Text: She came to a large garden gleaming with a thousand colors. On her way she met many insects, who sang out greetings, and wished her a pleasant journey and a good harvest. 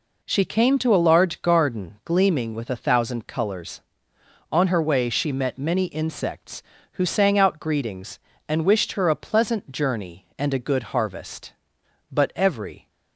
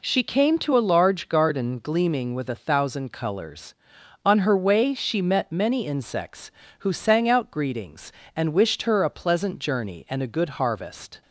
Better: second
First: goes on to say "But every"; noticeable; from 12.1 s on; 0.78 s long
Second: none

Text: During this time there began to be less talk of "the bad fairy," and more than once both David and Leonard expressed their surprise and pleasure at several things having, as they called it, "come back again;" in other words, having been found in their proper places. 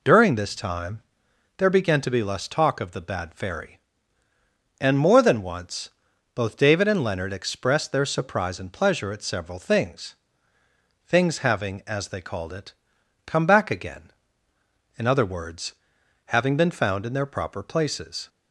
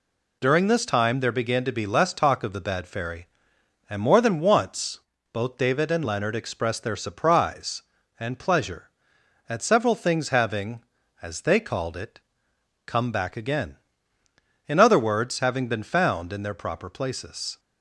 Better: second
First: pauses between "time" and "there"; noticeable; at 1.0 s; 0.56 s long // pauses between "once" and "both"; at 5.8 s; 0.44 s long // says "things" twice; at 11.0 s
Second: pauses between "once" and "both"; slight; at 4.9 s; 0.32 s long

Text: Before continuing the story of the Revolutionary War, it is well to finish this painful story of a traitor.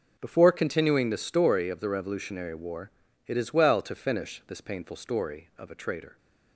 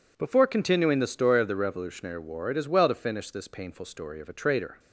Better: neither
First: none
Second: none

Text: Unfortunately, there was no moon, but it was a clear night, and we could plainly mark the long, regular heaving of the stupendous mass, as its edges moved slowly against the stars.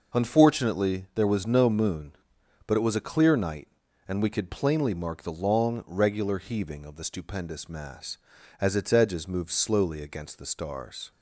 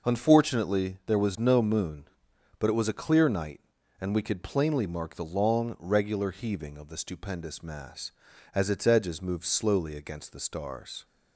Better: neither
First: none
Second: none

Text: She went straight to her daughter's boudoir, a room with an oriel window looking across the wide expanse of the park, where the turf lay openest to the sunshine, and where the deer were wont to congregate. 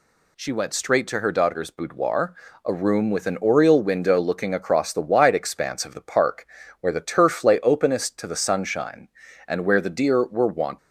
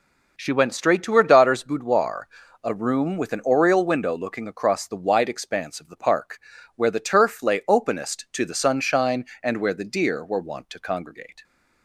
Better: second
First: stops before "to congregate"; at 10.7 s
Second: none

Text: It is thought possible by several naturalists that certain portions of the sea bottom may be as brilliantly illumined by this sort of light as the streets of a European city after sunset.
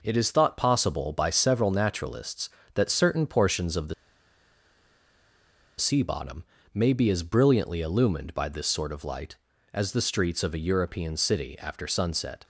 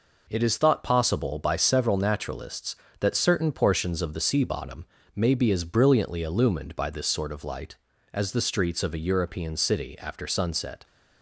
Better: second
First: pauses between "the" and "sea"; strong; at 3.9 s; 1.8 s long // pauses between "bottom" and "may"; slight; at 6.4 s; 0.30 s long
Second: pauses between "bottom" and "may"; slight; at 4.8 s; 0.30 s long

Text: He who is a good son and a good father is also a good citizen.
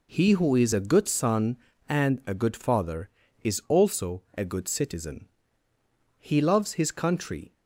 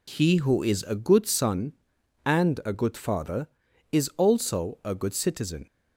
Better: second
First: goes on to say "He loves his country"; from 6.2 s on; 1.3 s long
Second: none

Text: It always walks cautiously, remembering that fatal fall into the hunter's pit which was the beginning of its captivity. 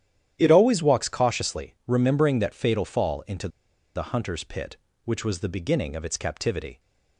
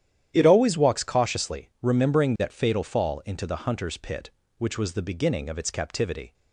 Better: second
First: starts louder than the rest; strong; until 1.3 s; 11 dB // pauses between "into" and "the"; noticeable; at 3.4 s; 0.46 s long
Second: starts louder than the rest; strong; until 1.3 s; 11 dB

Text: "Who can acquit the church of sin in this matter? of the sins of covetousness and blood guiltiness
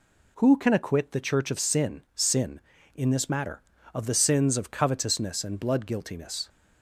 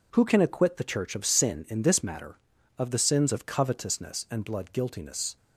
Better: second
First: says "sin" twice; at 2.1 s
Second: none

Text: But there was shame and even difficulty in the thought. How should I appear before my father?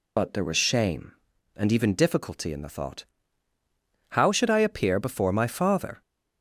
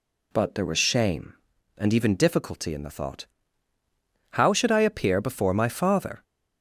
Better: second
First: loses the start of "But"; at 0.1 s; 50 ms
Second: none

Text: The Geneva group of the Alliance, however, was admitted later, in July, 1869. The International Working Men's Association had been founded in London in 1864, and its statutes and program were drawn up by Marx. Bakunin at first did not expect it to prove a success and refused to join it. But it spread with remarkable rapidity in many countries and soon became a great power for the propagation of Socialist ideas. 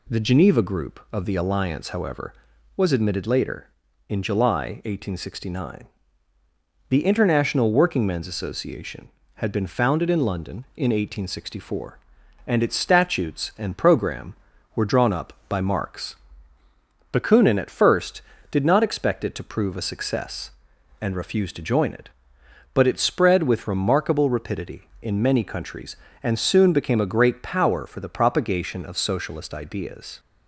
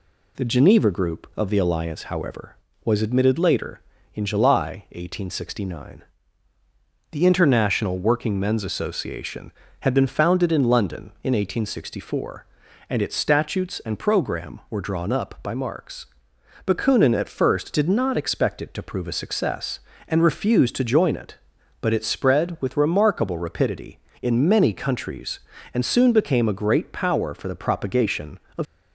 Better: first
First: none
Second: stops before "Socialist ideas"; at 28.6 s

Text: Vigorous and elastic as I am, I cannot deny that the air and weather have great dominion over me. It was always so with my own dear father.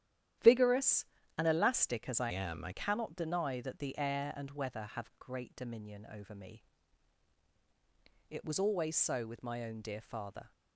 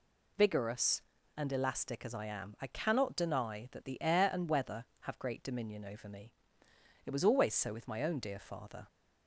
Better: second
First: starts louder than the rest; strong; until 1.7 s; 11.5 dB // changes voice from "am" to "I"; from 2.2 to 2.7 s; 0.5 s long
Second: none

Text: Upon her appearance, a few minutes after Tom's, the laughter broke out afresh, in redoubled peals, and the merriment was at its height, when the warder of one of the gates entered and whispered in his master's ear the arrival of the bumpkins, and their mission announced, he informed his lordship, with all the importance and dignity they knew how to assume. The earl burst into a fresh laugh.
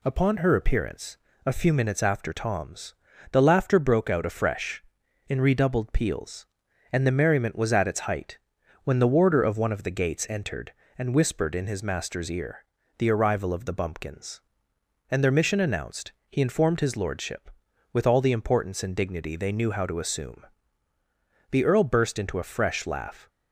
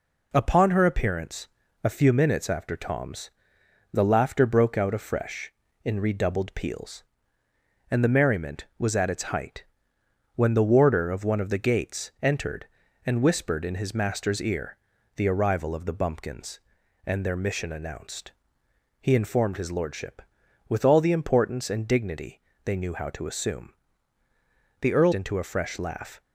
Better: first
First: pauses between "ear" and "the"; slight; at 12.6 s; 0.34 s long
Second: pauses between "ear" and "the"; at 14.7 s; 0.40 s long // pauses between "dignity" and "they"; slight; at 22.4 s; 0.22 s long // skips "burst"; at 25.1 s

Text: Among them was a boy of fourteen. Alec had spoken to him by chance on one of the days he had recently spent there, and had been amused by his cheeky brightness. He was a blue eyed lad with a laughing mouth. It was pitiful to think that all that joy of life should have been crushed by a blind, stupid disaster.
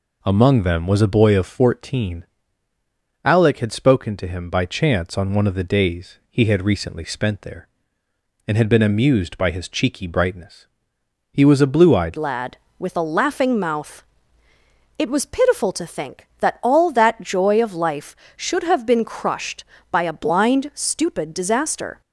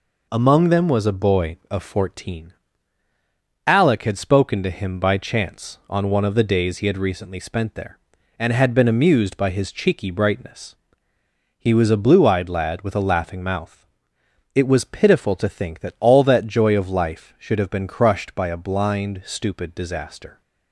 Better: second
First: changes voice at "lad"; from 12.1 s on; 9.9 s long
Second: none

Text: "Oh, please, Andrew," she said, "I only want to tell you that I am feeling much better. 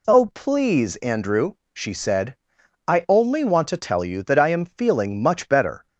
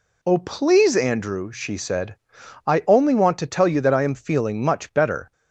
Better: neither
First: none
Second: none

